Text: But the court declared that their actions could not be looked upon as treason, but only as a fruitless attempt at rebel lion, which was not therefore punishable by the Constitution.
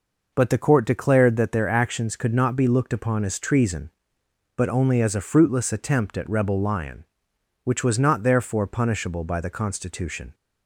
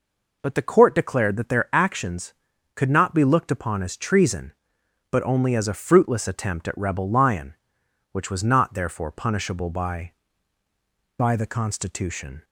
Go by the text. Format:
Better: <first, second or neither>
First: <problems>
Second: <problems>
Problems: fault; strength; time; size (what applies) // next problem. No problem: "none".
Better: first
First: none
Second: says "by" twice; at 11.1 s